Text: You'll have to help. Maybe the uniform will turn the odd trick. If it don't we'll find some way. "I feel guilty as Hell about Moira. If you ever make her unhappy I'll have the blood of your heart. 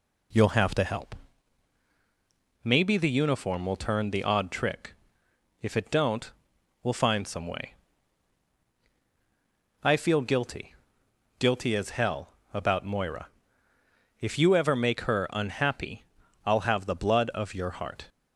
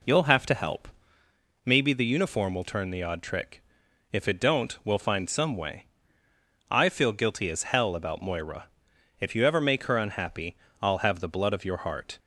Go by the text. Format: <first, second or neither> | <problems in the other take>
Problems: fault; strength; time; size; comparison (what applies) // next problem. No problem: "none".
second | pauses between "don't" and "we'll"; noticeable; at 6.3 s; 0.52 s long // says "guilty" twice; at 11.3 s // pauses between "Hell" and "about"; slight; at 12.2 s; 0.24 s long // pauses between "unhappy" and "I'll"; at 16.0 s; 0.40 s long; slight in the second